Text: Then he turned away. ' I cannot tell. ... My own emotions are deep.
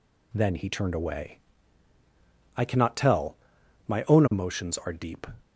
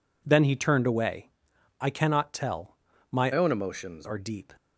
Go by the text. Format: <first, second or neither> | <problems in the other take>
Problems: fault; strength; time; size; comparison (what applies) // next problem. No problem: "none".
first | changes voice from "own" to "emotions"; from 3.3 to 4.0 s; 0.7 s long